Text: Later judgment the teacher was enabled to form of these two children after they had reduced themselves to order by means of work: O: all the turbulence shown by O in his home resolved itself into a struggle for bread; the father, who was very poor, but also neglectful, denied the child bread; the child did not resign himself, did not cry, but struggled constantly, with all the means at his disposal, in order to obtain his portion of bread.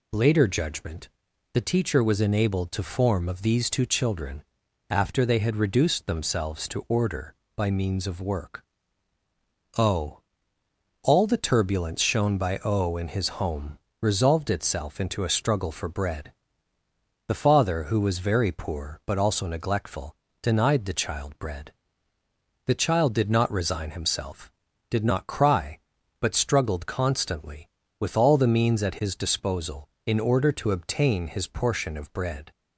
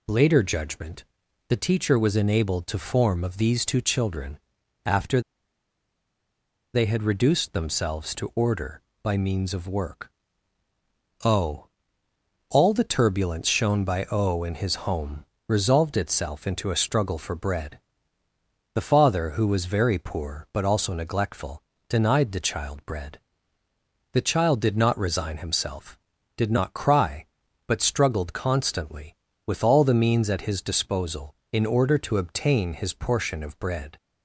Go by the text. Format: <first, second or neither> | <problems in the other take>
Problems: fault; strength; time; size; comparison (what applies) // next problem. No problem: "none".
first | pauses between "judgment" and "the"; at 1.0 s; 0.44 s long; also in the first // pauses between "children" and "after"; noticeable; at 4.3 s; 0.46 s long; noticeable in the first // pauses between "after" and "they"; strong; at 5.2 s; 1.5 s long // pauses between "home" and "resolved"; slight; at 15.2 s; 0.20 s long; slight in the first